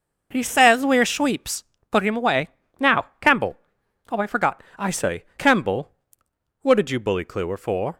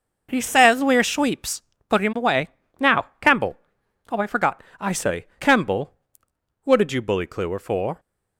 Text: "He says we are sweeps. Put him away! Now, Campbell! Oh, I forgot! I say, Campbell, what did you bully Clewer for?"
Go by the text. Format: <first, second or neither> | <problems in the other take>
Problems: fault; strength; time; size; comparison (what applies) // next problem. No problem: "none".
neither | none